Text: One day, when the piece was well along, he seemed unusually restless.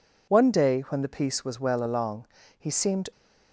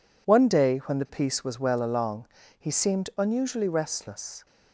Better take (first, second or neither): second